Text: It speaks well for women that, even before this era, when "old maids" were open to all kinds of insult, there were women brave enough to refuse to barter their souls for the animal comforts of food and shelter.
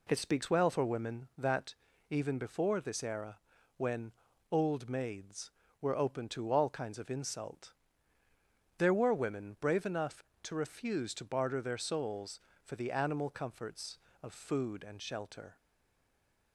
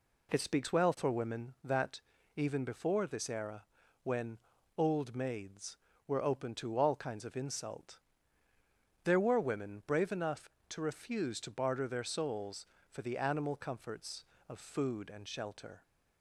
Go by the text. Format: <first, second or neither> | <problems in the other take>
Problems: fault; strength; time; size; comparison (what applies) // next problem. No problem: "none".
second | pauses between "when" and "old"; at 4.1 s; 0.40 s long; also in the second // stays silent after the last word; from 15.5 s on; 1.0 s long